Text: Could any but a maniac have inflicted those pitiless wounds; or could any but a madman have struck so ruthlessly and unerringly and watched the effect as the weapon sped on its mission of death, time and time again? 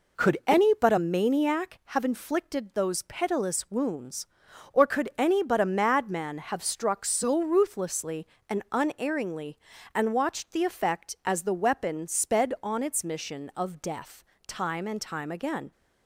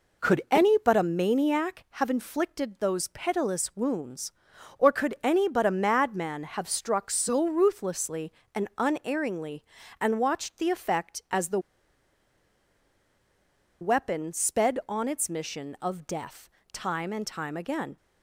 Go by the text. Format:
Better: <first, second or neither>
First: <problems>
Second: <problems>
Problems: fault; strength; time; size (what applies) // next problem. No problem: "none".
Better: first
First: none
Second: pauses between "the" and "weapon"; strong; at 11.5 s; 2.2 s long